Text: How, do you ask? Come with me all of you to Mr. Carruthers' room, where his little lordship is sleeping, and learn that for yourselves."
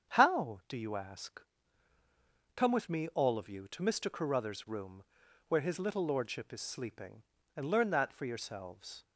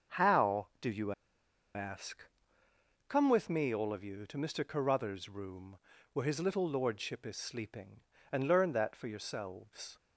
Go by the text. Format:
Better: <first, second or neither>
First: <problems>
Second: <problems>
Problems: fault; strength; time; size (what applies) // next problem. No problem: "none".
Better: first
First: starts louder than the rest; strong; until 1.1 s; 8 dB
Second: starts louder than the rest; until 1.8 s; 6.5 dB // pauses between "you" and "ask"; noticeable; at 1.1 s; 0.62 s long